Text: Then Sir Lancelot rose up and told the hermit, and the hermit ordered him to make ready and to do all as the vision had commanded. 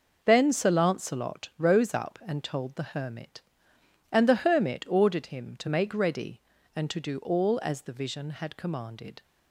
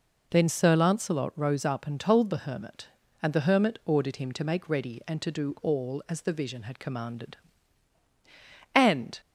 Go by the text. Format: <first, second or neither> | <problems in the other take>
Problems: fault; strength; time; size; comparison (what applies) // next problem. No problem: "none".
first | goes on to say "And"; slight; from 8.7 s on; 0.46 s long